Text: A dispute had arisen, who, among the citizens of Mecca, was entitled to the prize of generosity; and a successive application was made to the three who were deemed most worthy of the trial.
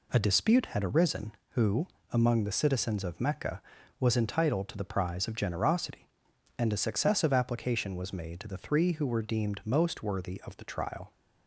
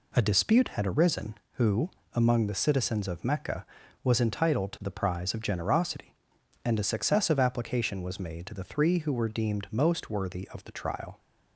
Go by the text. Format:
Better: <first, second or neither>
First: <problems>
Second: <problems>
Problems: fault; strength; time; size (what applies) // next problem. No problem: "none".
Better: neither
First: none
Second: none